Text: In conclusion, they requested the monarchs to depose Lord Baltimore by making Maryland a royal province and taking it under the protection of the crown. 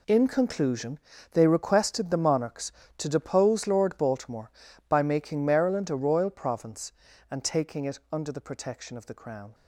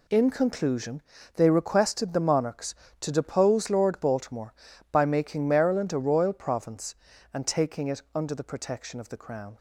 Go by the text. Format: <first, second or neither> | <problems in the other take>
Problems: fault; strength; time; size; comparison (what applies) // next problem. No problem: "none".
second | gets quieter; strong; throughout; 13 dB